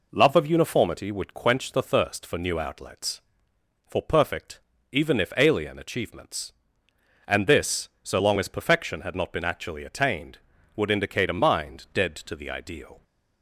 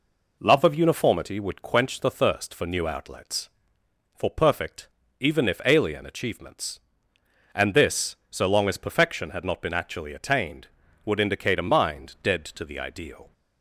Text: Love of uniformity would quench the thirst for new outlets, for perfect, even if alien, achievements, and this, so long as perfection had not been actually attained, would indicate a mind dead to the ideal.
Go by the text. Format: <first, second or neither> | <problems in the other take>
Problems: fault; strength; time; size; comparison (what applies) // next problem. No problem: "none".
neither | none